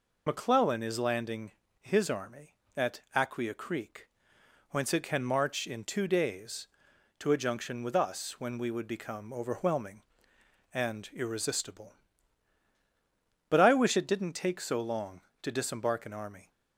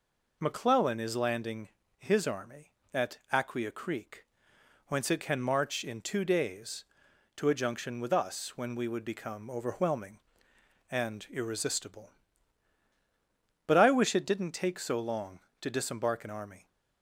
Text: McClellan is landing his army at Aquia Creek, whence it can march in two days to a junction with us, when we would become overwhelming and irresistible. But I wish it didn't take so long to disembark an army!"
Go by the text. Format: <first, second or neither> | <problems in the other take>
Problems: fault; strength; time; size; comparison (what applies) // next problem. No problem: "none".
second | loses the start of "McClellan"; at 0.2 s; 40 ms // pauses between "landing" and "his"; slight; at 1.5 s; 0.30 s long; slight in the second